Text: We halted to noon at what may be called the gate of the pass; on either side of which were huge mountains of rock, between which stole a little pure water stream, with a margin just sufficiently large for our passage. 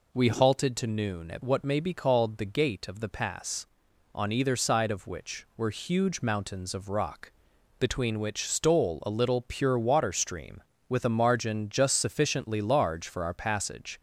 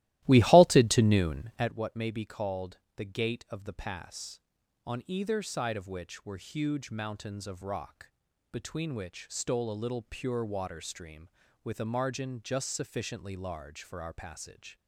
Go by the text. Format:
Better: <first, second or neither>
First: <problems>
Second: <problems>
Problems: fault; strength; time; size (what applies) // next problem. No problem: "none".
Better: first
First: none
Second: starts louder than the rest; strong; until 1.7 s; 16 dB // pauses between "called" and "the"; slight; at 2.7 s; 0.16 s long